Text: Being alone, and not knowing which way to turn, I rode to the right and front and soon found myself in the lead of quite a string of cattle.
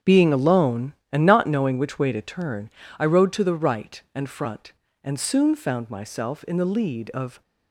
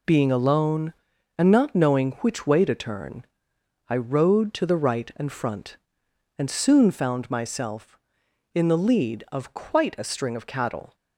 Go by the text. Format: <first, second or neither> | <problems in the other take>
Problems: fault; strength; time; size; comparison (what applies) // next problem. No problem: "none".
second | starts louder than the rest; strong; until 1.2 s; 7.5 dB // stops before "quite a string of cattle"; at 7.4 s